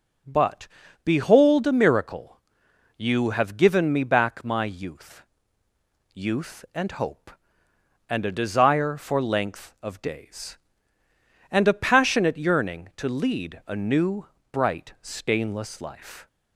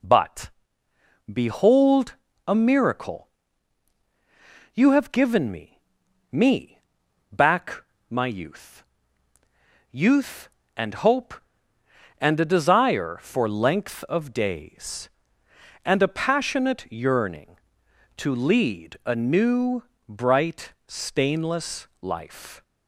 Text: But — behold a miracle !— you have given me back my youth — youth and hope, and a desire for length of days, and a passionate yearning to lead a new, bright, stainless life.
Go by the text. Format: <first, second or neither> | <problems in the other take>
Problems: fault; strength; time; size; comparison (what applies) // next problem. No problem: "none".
first | pauses between "behold" and "a"; slight; at 2.1 s; 0.32 s long // says "me" twice; at 6.3 s // pauses between "back" and "my"; slight; at 7.8 s; 0.26 s long